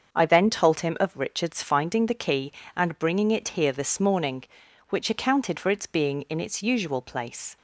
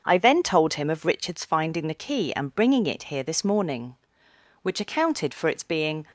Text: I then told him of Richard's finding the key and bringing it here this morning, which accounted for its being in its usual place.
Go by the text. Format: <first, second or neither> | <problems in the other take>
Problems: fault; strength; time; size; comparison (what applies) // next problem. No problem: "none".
first | starts louder than the rest; until 1.0 s; 6.5 dB; also in the first // stops before "in its usual place"; at 6.0 s